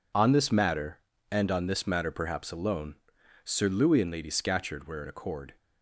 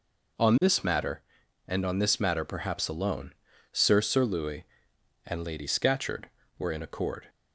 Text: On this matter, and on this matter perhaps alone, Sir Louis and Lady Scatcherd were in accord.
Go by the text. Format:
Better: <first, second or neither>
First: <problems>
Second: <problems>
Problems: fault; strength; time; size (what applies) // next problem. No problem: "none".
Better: first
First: none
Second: says "Sir" twice; at 4.0 s